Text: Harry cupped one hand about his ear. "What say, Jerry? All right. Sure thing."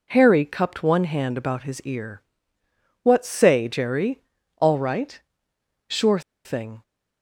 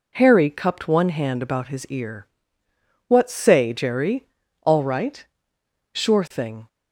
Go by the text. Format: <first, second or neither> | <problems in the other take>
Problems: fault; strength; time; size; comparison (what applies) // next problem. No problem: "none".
second | pauses between "Sure" and "thing"; slight; at 6.1 s; 0.25 s long